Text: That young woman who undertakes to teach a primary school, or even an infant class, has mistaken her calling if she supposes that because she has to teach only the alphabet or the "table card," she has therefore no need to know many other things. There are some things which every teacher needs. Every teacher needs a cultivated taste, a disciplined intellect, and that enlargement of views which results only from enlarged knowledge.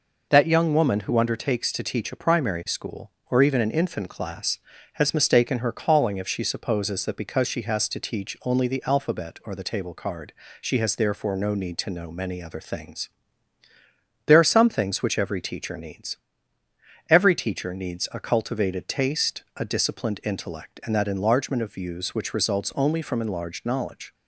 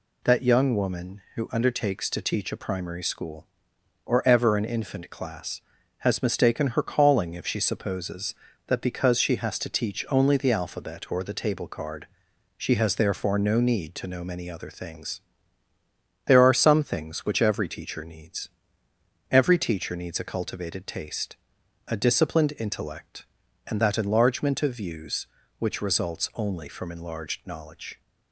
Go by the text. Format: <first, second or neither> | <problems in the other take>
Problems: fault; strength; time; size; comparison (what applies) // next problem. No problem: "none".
first | says "ever" for "even"; at 4.2 s